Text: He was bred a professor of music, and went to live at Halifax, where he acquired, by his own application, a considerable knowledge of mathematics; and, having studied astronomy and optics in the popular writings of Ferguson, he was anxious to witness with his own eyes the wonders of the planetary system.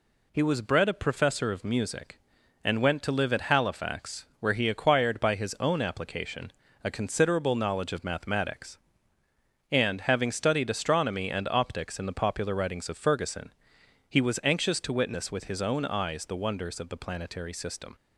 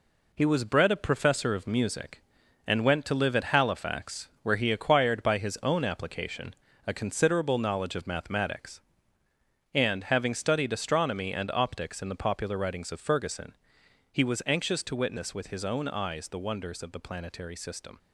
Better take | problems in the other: first | gets quieter; noticeable; throughout; 5.5 dB

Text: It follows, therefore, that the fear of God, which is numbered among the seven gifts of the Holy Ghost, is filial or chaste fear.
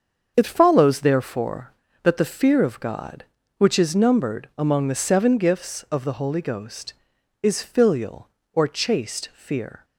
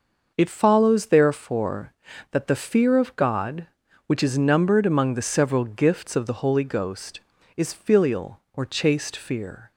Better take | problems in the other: first | starts louder than the rest; noticeable; until 1.3 s; 6 dB; also in the first // says "several" for "seven"; at 5.2 s

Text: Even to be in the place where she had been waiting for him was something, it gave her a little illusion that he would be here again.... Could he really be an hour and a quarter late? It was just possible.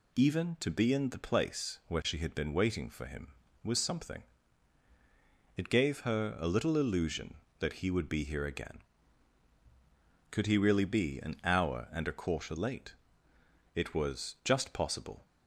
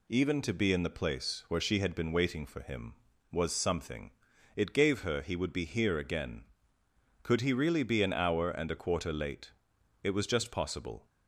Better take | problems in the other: first | skips "a little illusion that"; at 5.2 s

